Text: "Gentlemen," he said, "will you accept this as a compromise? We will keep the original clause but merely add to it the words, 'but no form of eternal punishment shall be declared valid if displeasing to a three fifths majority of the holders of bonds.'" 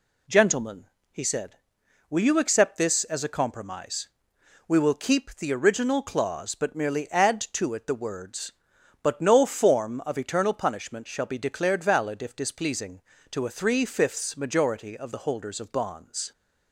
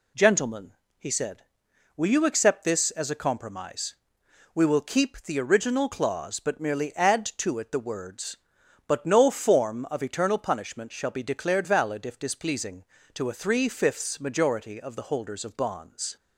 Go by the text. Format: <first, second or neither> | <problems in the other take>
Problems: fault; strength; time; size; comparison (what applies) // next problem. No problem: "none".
neither | none